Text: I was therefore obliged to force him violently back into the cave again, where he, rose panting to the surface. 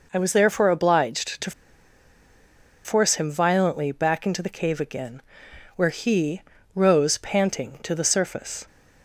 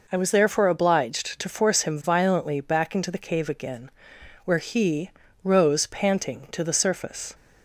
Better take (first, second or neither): second